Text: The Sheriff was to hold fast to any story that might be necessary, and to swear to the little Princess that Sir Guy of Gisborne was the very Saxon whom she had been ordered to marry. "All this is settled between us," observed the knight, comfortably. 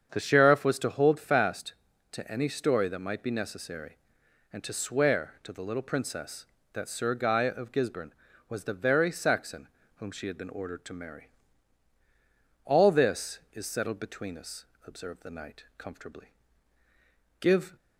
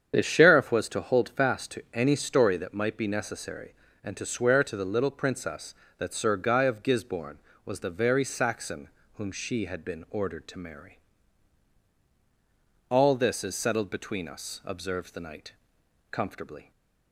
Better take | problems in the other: second | starts louder than the rest; strong; until 1.1 s; 7.5 dB; strong in the second // pauses between "Saxon" and "whom"; slight; at 9.6 s; 0.30 s long; slight in the second // goes on to say "Give"; slight; from 17.3 s on; 0.36 s long

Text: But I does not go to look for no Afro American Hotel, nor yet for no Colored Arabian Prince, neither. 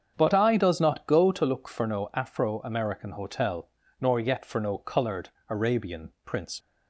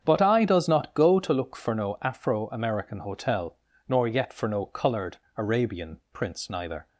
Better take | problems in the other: second | starts louder than the rest; strong; until 1.1 s; 7.5 dB; strong in the second // pauses between "Colored" and "Arabian"; slight; at 5.2 s; 0.20 s long; slight in the second // stops before "neither"; at 6.6 s

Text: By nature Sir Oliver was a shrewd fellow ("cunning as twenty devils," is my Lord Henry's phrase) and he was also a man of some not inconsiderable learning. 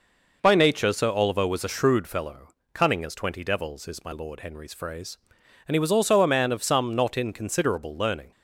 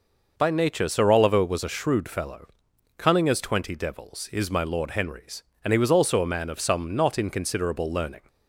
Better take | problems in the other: first | skips "phrase"; at 5.5 s

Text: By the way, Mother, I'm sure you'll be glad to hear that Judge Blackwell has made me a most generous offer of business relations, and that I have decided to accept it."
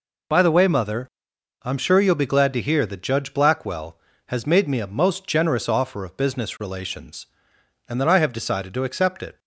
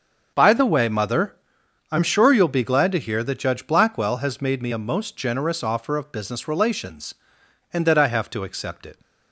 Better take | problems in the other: first | starts louder than the rest; until 1.3 s; 6.5 dB // skips "decided"; at 8.3 s

